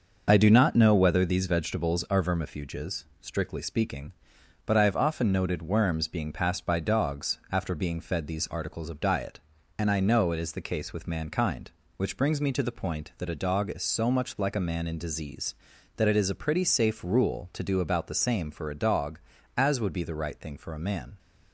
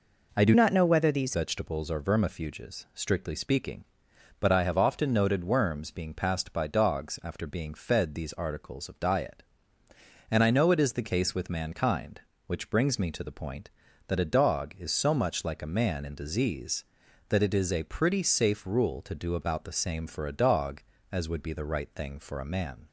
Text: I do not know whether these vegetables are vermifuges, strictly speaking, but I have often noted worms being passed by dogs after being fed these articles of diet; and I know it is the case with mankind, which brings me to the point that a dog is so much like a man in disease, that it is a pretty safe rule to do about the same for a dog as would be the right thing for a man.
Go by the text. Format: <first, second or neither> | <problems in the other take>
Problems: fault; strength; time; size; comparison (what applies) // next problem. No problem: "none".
first | changes voice from "not" to "these"; from 0.5 to 1.3 s; 0.8 s long